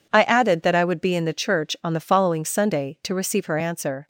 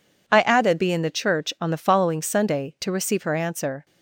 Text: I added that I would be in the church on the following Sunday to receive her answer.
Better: first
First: none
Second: skips "that I would"; at 0.7 s

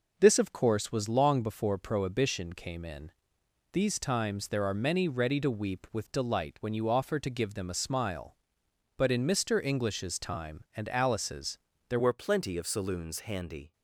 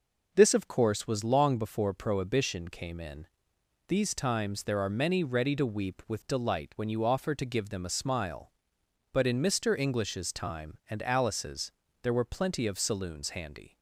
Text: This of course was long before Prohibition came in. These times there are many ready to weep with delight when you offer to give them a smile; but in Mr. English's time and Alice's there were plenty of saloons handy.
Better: second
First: pauses between "Alice's" and "there"; slight; at 11.5 s; 0.32 s long // changes voice at "were"; from 11.9 s on; 1.8 s long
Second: pauses between "Alice's" and "there"; slight; at 11.7 s; 0.32 s long

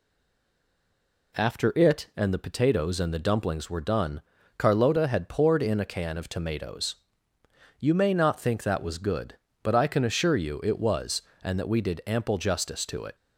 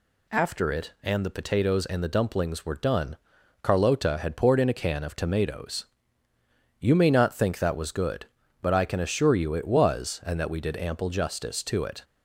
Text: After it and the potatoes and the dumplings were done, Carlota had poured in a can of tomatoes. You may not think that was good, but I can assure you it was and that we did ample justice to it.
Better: second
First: stays silent before the first word; noticeable; until 1.3 s; 1.3 s long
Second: none

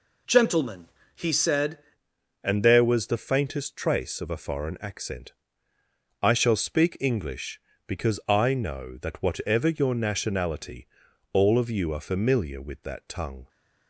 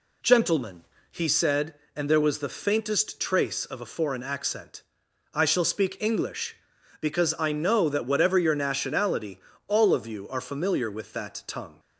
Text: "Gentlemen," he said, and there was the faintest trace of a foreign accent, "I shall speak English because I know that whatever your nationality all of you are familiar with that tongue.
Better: second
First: changes voice at "and"; from 2.4 s on; 11.0 s long // pauses between "nationality" and "all"; noticeable; at 10.8 s; 0.46 s long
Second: pauses between "nationality" and "all"; slight; at 9.3 s; 0.28 s long

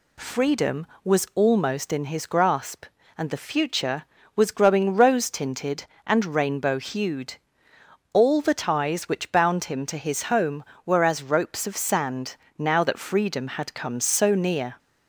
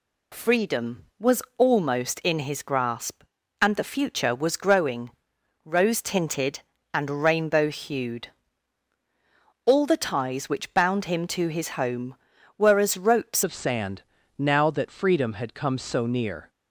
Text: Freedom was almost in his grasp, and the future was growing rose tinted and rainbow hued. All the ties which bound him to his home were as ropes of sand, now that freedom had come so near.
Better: first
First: none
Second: pauses between "was" and "almost"; slight; at 1.4 s; 0.16 s long // pauses between "growing" and "rose"; noticeable; at 5.1 s; 0.52 s long // changes voice at "of"; from 13.4 s on; 3.0 s long

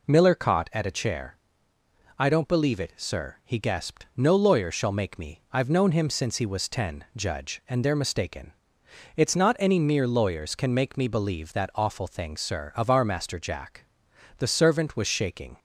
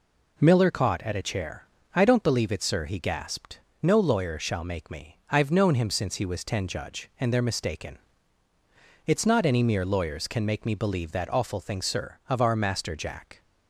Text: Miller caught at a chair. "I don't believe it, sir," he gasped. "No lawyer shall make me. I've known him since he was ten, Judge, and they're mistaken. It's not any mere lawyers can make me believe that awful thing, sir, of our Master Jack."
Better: second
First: goes on to say "The servant was shaking"; noticeable; from 14.3 s on; 1.2 s long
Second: none

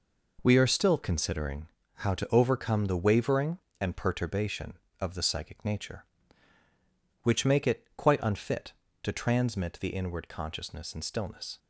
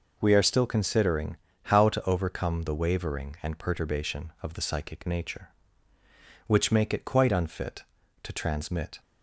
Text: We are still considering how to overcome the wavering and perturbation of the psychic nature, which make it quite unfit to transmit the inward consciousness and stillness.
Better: first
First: pauses between "considering" and "how"; slight; at 1.6 s; 0.28 s long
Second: pauses between "considering" and "how"; slight; at 1.3 s; 0.26 s long // stops before "the inward consciousness and stillness"; at 8.9 s

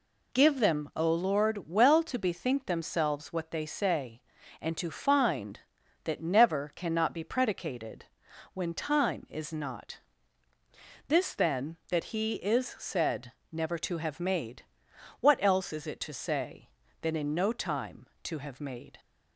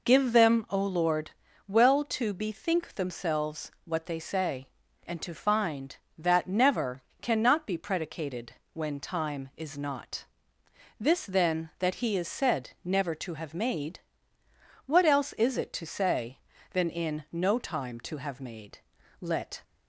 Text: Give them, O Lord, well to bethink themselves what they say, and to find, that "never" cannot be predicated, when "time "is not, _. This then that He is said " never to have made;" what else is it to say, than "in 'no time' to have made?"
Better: first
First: none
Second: pauses between "never" and "cannot"; slight; at 7.0 s; 0.18 s long // goes on to say "Let"; slight; from 19.2 s on; 0.42 s long

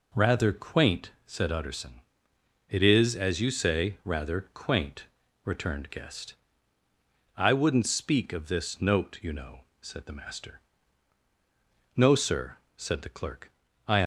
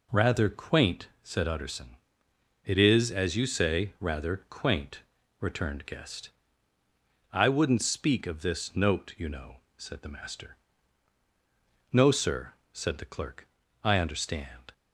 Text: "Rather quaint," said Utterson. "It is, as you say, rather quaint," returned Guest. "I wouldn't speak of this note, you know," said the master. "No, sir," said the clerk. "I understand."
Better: second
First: stops before "understand"; at 14.0 s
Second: none

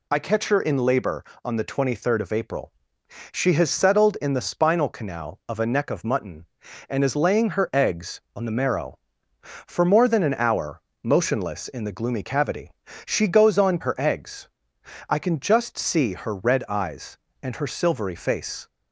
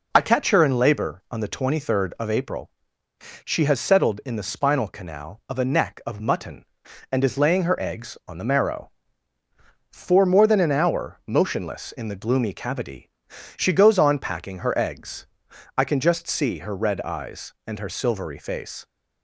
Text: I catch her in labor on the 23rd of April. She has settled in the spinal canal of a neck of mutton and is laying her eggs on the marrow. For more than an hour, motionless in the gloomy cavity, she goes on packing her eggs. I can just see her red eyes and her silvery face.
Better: second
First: skips "packing"; at 13.8 s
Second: none

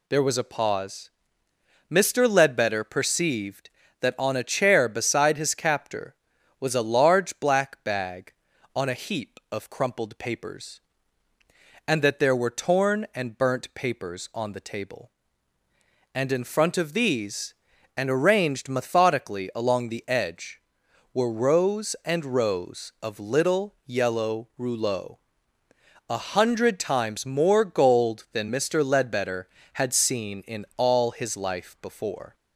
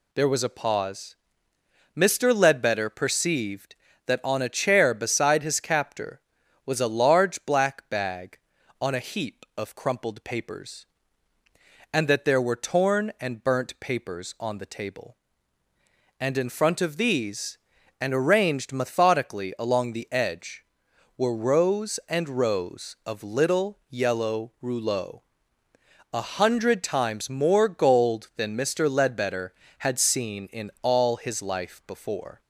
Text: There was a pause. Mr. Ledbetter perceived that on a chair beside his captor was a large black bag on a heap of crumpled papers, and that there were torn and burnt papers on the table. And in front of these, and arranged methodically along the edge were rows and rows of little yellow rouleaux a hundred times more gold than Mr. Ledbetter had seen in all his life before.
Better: neither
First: pauses between "rouleaux" and "a"; noticeable; at 25.1 s; 0.94 s long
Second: pauses between "rouleaux" and "a"; noticeable; at 25.1 s; 0.94 s long

